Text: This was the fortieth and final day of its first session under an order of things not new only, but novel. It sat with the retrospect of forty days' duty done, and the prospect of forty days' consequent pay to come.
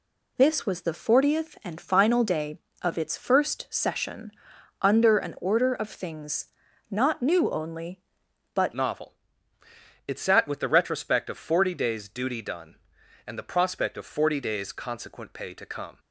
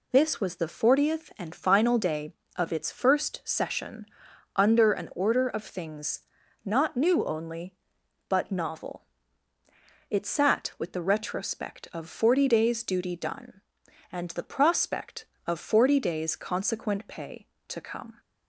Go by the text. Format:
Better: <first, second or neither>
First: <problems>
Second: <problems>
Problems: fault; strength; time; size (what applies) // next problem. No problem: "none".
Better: second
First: pauses between "session" and "under"; noticeable; at 4.3 s; 0.50 s long // pauses between "things" and "not"; at 6.4 s; 0.44 s long // changes voice at "novel"; from 8.7 s on; 7.2 s long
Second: pauses between "session" and "under"; noticeable; at 4.0 s; 0.50 s long // pauses between "things" and "not"; at 6.2 s; 0.44 s long